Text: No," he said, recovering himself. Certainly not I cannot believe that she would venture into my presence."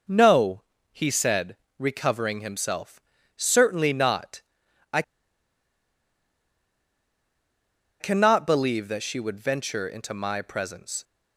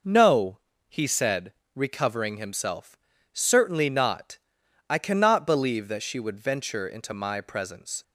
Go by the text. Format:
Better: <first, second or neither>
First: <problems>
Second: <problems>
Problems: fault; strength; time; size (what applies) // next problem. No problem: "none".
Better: second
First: pauses between "not" and "I"; noticeable; at 4.3 s; 0.54 s long // pauses between "I" and "cannot"; strong; at 5.0 s; 2.9 s long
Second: pauses between "not" and "I"; noticeable; at 4.3 s; 0.54 s long